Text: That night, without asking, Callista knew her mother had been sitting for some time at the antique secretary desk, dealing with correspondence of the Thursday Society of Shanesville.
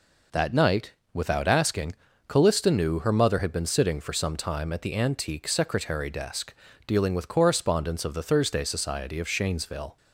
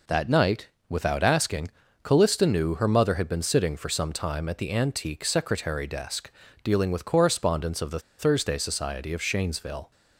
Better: first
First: none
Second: pauses between "the" and "Thursday"; slight; at 7.9 s; 0.19 s long

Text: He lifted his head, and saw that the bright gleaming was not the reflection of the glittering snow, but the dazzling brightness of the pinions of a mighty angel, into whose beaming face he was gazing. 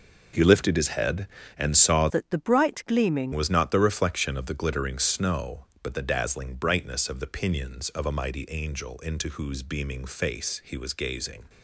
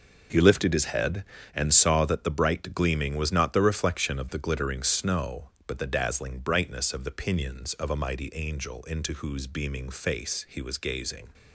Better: second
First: changes voice from "that" to "gleaming"; from 2.0 to 3.3 s; 1.3 s long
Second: none

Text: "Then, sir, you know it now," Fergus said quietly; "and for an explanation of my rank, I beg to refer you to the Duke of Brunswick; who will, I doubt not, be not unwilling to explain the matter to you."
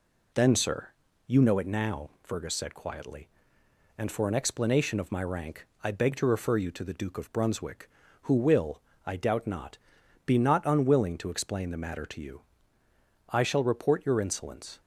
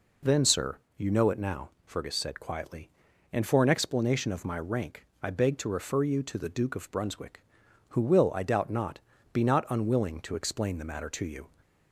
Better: second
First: goes on to say "I shall report your insolence"; from 13.3 s on; 1.5 s long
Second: none

